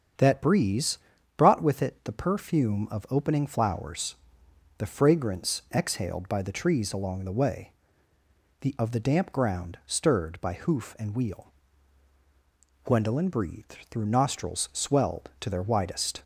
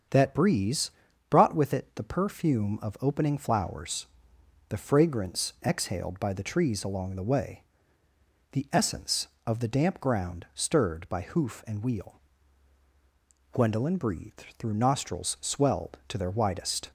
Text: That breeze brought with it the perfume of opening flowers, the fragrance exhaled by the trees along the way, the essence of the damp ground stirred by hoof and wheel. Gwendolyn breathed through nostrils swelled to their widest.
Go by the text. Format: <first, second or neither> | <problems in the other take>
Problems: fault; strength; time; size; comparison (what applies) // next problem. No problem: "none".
second | starts louder than the rest; strong; until 1.5 s; 8 dB; strong in the second // pauses between "breeze" and "brought"; at 0.9 s; 0.40 s long; also in the second // skips "essence"; at 8.7 s